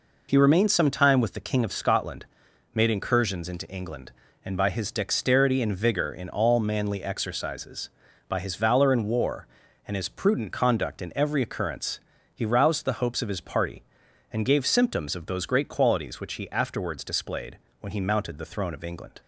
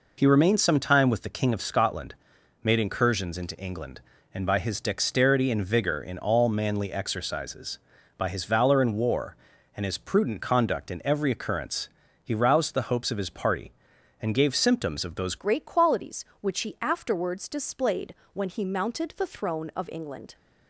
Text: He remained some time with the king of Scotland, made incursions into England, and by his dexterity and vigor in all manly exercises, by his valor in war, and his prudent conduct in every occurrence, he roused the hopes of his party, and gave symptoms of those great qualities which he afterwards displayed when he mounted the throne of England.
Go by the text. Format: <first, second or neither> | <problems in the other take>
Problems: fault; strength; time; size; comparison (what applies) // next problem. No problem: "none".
first | changes voice at "great"; from 15.3 s on; 5.0 s long // pauses between "displayed" and "when"; slight; at 18.1 s; 0.20 s long; slight in the first